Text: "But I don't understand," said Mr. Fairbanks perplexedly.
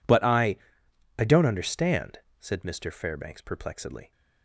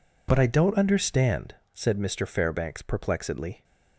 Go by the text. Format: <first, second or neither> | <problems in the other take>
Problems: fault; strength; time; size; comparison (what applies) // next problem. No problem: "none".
second | says "I" twice; at 1.1 s